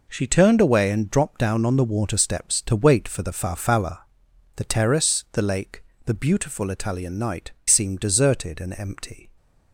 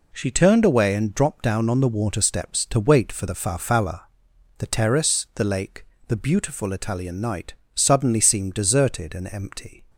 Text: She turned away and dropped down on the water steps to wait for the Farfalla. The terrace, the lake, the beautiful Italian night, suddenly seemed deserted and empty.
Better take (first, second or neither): second